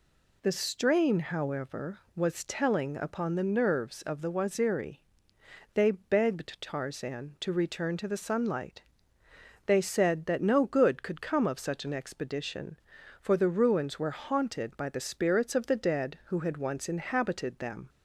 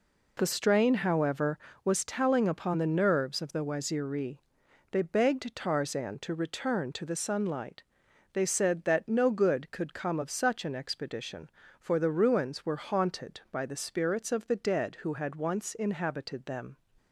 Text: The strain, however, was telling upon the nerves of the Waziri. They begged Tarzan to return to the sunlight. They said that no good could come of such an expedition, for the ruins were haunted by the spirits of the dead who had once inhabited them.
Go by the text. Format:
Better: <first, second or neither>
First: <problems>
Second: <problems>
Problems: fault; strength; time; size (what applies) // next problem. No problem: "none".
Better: neither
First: none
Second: none